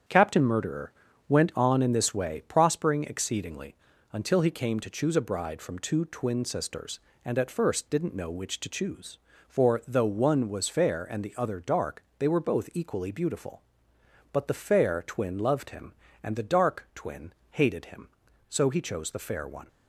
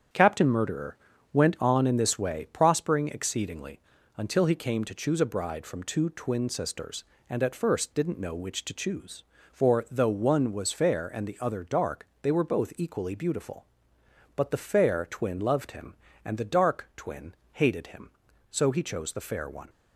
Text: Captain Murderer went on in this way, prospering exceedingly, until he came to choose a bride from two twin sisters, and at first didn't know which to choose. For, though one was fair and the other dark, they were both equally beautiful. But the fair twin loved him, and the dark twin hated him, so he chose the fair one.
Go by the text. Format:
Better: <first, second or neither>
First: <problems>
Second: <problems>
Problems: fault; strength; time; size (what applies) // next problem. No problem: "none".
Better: neither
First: starts louder than the rest; strong; until 1.4 s; 8.5 dB // pauses between "Murderer" and "went"; slight; at 0.9 s; 0.36 s long // pauses between "twin" and "hated"; slight; at 17.3 s; 0.18 s long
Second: starts louder than the rest; strong; until 1.4 s; 8.5 dB // pauses between "Murderer" and "went"; slight; at 0.9 s; 0.36 s long // pauses between "twin" and "hated"; slight; at 17.3 s; 0.18 s long